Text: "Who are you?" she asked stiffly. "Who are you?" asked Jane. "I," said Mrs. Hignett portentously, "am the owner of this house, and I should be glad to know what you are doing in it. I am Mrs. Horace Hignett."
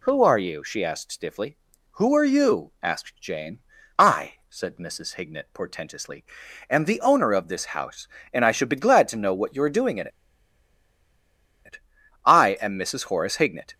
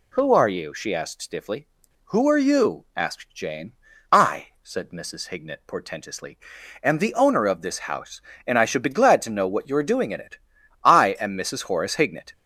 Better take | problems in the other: second | pauses between "in" and "it"; strong; at 10.0 s; 1.5 s long

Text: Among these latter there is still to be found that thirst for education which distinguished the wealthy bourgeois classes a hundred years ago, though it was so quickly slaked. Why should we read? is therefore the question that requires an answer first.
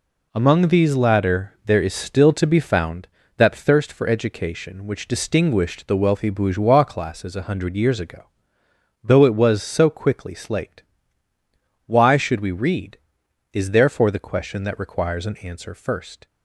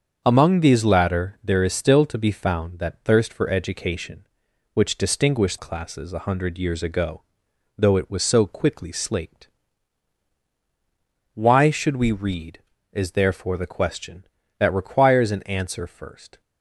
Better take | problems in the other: first | starts louder than the rest; until 1.2 s; 7 dB // skips "the wealthy bourgeois"; at 5.5 s

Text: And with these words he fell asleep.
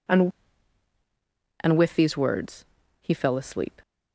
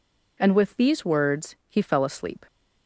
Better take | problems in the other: second | says "And" twice; at 1.6 s // pauses between "words" and "he"; at 2.6 s; 0.38 s long

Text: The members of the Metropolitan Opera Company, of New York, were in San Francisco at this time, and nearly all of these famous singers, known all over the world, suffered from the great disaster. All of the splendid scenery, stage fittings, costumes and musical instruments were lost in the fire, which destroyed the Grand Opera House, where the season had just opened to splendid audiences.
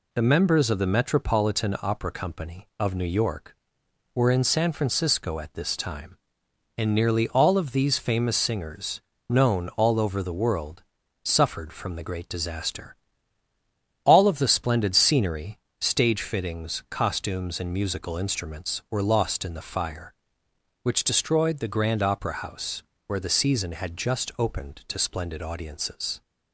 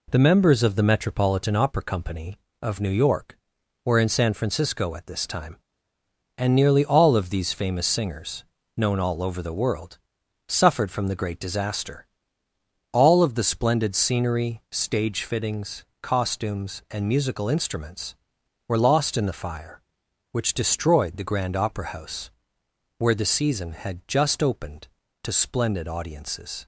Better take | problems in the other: neither | none

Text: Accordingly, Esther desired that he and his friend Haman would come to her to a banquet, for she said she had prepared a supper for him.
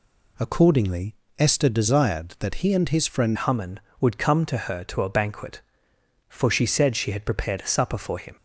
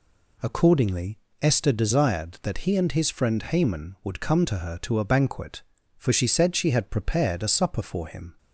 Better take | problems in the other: second | changes voice at "Haman"; from 3.3 s on; 5.0 s long

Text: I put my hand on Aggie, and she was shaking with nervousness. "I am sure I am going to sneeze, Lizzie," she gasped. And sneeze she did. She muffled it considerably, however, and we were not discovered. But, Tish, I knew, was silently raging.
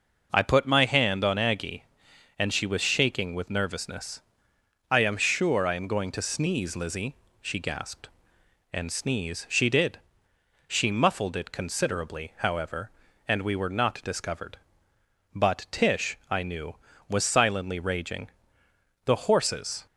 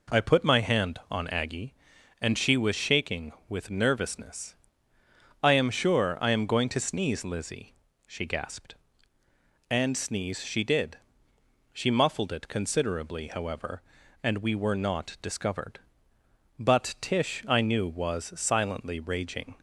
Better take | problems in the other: second | goes on to say "The horses"; noticeable; from 19.0 s on; 0.80 s long

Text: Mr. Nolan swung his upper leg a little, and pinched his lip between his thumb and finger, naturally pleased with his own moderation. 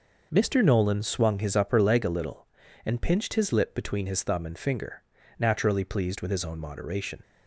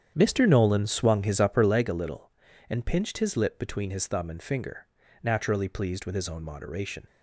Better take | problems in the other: first | starts louder than the rest; strong; until 1.8 s; 9 dB

